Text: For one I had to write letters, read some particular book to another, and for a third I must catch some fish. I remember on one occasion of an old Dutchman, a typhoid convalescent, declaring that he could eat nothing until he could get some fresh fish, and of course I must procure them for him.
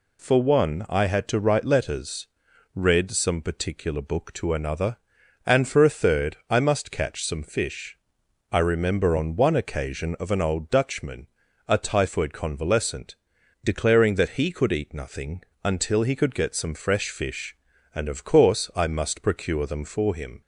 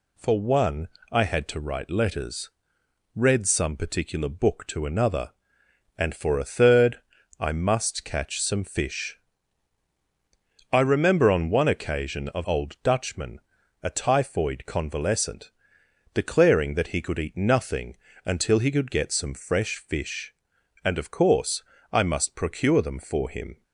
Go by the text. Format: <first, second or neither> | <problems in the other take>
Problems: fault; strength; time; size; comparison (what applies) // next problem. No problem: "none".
first | pauses between "one" and "I"; slight; at 0.8 s; 0.24 s long // pauses between "third" and "I"; at 6.9 s; 0.40 s long // skips "an"; at 12.4 s // pauses between "nothing" and "until"; slight; at 17.9 s; 0.28 s long; slight in the first // pauses between "course" and "I"; slight; at 21.6 s; 0.30 s long